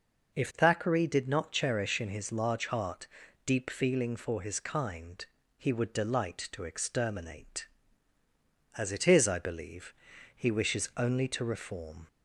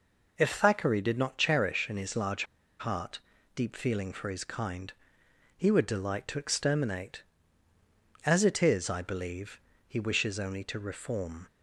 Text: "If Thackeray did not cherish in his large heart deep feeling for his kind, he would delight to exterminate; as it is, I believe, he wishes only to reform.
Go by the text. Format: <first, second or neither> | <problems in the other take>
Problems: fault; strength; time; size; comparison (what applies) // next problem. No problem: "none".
first | pauses between "large" and "heart"; slight; at 2.4 s; 0.34 s long // pauses between "heart" and "deep"; slight; at 3.2 s; 0.34 s long; also in the first